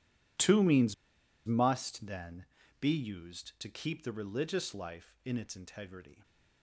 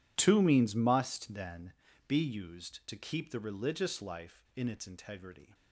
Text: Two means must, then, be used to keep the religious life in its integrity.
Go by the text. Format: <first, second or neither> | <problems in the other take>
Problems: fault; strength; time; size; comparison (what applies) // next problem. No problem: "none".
second | pauses between "means" and "must"; noticeable; at 0.9 s; 0.52 s long